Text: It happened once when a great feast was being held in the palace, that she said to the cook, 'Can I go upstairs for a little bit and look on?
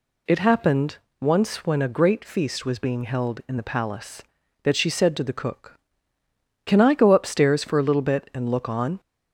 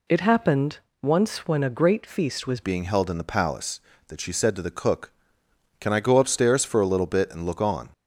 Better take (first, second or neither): first